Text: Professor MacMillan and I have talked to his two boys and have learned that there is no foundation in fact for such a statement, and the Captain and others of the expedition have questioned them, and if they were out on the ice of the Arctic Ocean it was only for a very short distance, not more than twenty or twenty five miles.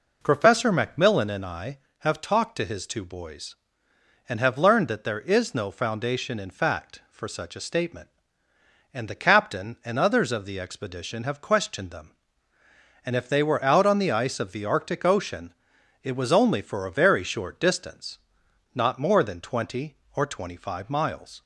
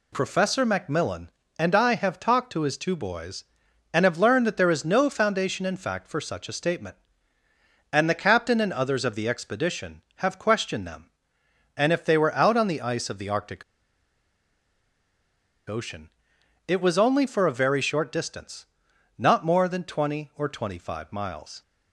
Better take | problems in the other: first | pauses between "Arctic" and "Ocean"; strong; at 13.6 s; 2.0 s long // pauses between "Ocean" and "it"; noticeable; at 16.0 s; 0.56 s long; noticeable in the first

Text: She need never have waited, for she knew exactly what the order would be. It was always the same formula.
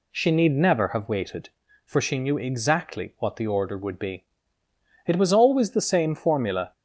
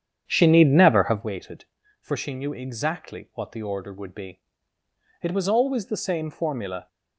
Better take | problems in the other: first | starts louder than the rest; strong; until 1.3 s; 8.5 dB

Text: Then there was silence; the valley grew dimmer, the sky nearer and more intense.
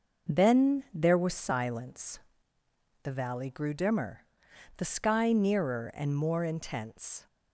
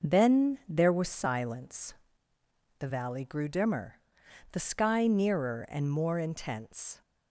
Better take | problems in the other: neither | none

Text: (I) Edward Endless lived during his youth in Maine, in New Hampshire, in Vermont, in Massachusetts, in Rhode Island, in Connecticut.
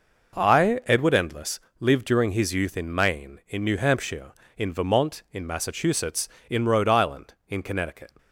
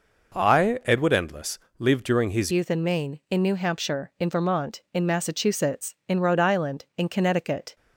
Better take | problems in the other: first | pauses between "Endless" and "lived"; slight; at 1.5 s; 0.18 s long; slight in the first // changes voice at "youth"; from 2.4 s on; 5.3 s long

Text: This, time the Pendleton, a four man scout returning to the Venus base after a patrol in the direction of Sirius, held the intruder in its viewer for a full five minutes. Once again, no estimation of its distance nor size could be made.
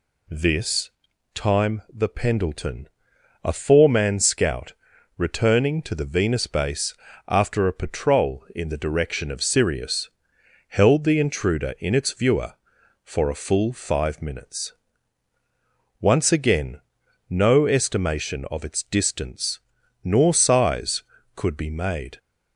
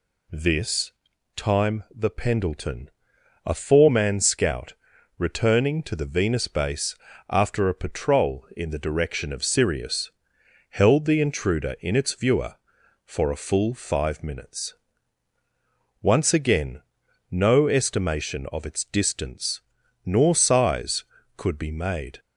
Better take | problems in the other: neither | pauses between "scout" and "returning"; the same in both // pauses between "base" and "after"; slight; the same in both // pauses between "distance" and "nor"; the same in both

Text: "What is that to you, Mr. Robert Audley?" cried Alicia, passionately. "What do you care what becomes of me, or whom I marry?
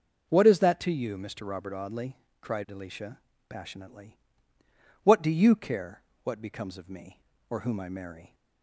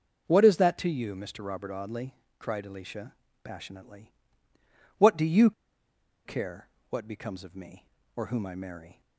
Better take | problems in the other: first | pauses between "you" and "care"; noticeable; at 5.5 s; 0.74 s long // pauses between "care" and "what"; slight; at 6.6 s; 0.20 s long; slight in the first

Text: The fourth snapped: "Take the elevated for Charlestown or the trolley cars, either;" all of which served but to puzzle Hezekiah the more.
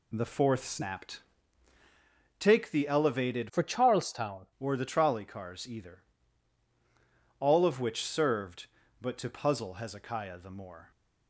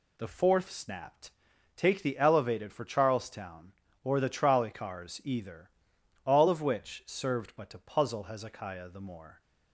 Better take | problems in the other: second | changes voice from "for" to "Charlestown"; from 3.4 to 4.4 s; 1.0 s long

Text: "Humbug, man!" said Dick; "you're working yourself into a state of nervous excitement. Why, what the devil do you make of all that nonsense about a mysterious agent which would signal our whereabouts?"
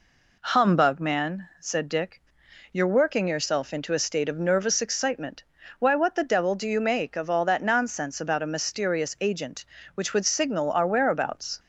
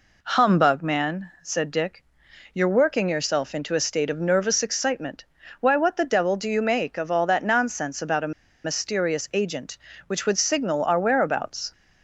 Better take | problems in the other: first | pauses between "a" and "mysterious"; slight; at 8.3 s; 0.32 s long

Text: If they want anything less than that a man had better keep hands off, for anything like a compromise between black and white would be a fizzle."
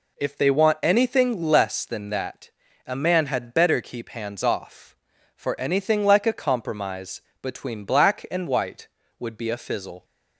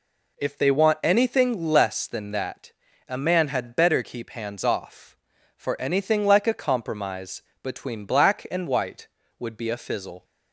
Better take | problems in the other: neither | pauses between "that" and "a"; slight; the same in both // pauses between "compromise" and "between"; slight; the same in both

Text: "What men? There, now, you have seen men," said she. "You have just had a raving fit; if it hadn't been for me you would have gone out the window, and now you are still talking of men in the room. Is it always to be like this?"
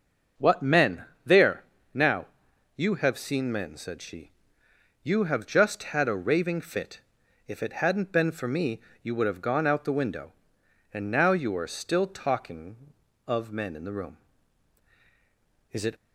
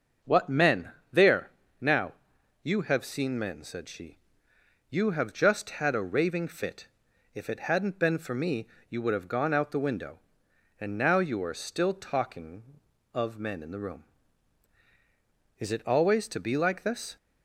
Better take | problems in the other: second | starts louder than the rest; noticeable; until 1.5 s; 6 dB; noticeable in the second // pauses between "me" and "you"; slight; at 8.8 s; 0.20 s long; slight in the second // stops before "always to be like this"; at 15.9 s

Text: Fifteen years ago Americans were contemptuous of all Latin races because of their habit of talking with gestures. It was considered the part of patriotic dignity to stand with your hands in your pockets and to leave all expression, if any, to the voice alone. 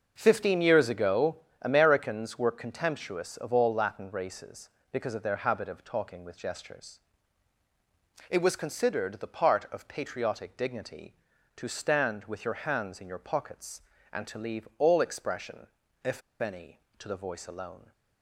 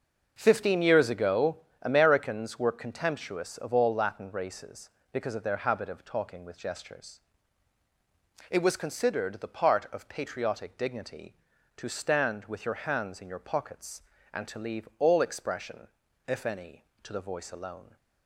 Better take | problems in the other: second | starts louder than the rest; until 1.1 s; 6 dB; also in the second // pauses between "ago" and "Americans"; slight; at 1.3 s; 0.24 s long; slight in the second // pauses between "if" and "any"; slight; at 16.2 s; 0.20 s long

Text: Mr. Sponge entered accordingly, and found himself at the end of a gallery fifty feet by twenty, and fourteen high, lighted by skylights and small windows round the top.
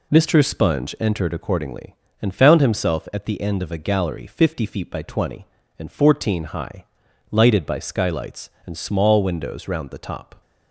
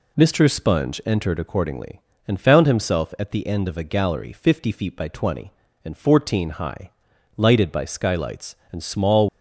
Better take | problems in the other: first | stops before "windows round the top"; at 9.2 s

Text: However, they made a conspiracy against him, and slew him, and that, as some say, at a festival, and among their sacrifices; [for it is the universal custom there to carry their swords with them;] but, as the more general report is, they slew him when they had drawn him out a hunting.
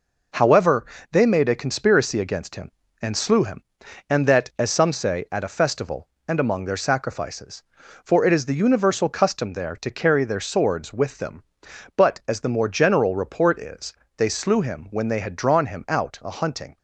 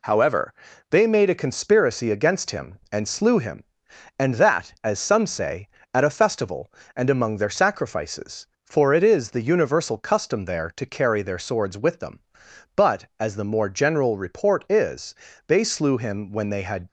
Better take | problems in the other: first | stops before "drawn him out a hunting"; at 16.8 s

